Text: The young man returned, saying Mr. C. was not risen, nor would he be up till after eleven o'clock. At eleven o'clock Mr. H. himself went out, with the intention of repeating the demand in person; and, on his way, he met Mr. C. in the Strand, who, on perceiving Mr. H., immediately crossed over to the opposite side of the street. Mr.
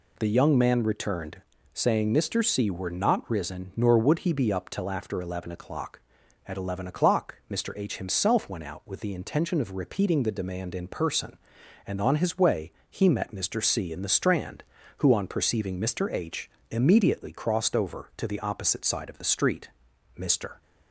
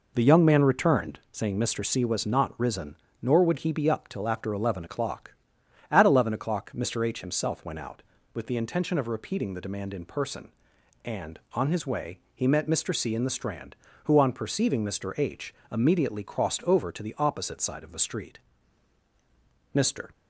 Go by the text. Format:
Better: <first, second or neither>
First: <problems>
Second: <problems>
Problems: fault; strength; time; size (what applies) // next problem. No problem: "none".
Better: second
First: says "were" for "was"; at 2.7 s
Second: none